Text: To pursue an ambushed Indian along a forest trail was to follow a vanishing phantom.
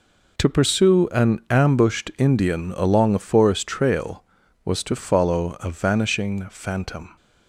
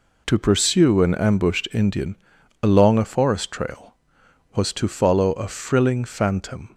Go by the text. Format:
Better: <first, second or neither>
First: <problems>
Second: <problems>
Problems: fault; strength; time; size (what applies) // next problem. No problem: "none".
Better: first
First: none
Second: pauses between "Indian" and "along"; noticeable; at 2.1 s; 0.46 s long // says "frilling" for "vanishing"; at 5.4 s